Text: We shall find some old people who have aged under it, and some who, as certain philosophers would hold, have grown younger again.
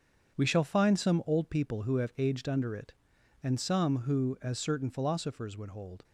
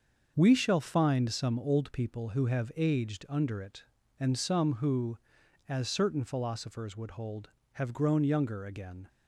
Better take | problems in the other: second | starts louder than the rest; strong; until 1.4 s; 7.5 dB; also in the second // stops before "have grown younger again"; at 6.0 s

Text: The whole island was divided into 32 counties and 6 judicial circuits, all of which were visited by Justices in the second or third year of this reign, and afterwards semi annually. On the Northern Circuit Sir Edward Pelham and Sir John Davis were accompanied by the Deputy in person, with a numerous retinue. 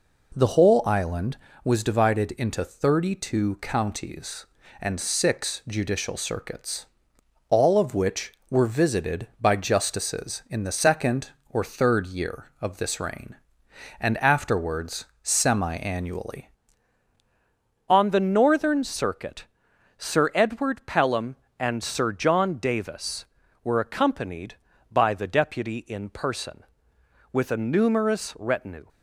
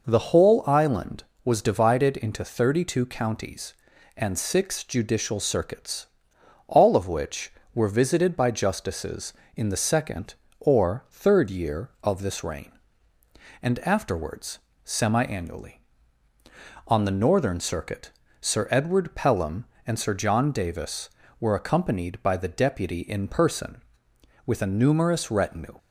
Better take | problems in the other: second | pauses between "afterwards" and "semi"; slight; at 15.0 s; 0.16 s long; slight in the second // changes voice at "On"; from 17.8 s on; 11.0 s long // pauses between "Circuit" and "Sir"; noticeable; at 19.4 s; 0.50 s long; slight in the second

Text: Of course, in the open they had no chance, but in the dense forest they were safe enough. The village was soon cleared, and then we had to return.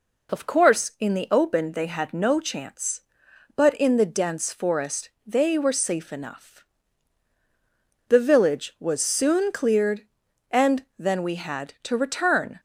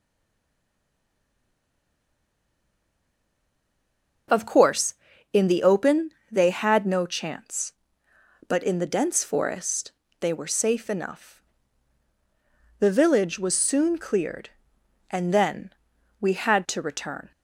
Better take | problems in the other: first | stays silent before the first word; strong; until 4.2 s; 4.2 s long // pauses between "open" and "they"; slight; at 6.1 s; 0.20 s long // pauses between "forest" and "they"; slight; at 9.9 s; 0.28 s long; slight in the first // pauses between "then" and "we"; noticeable; at 15.7 s; 0.48 s long

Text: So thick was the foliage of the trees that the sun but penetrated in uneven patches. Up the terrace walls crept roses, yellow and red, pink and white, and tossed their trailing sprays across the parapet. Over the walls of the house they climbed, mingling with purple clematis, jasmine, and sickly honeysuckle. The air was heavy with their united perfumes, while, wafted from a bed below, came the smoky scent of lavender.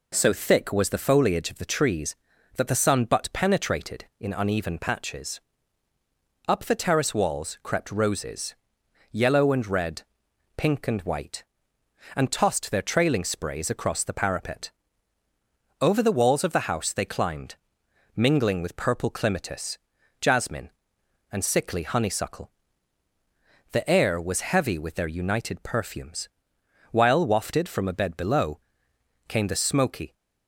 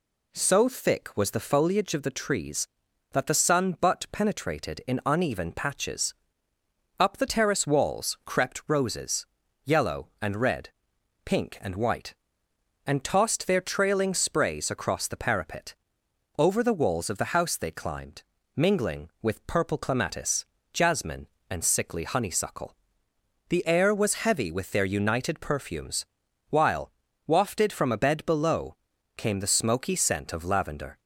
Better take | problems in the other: second | stops before "scent of lavender"; at 30.1 s

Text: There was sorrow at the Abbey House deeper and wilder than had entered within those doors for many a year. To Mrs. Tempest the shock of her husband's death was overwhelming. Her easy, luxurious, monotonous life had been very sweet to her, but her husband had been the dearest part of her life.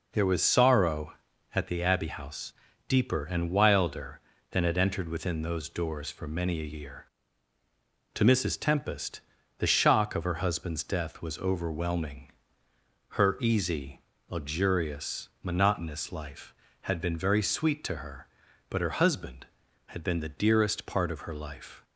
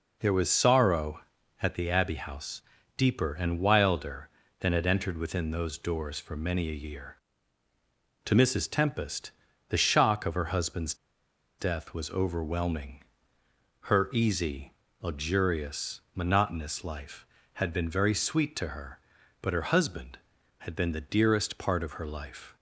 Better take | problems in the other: first | pauses between "House" and "deeper"; slight; at 2.6 s; 0.34 s long; slight in the first // pauses between "Tempest" and "the"; at 9.3 s; 0.38 s long; also in the first // pauses between "husband's" and "death"; noticeable; at 10.9 s; 0.64 s long

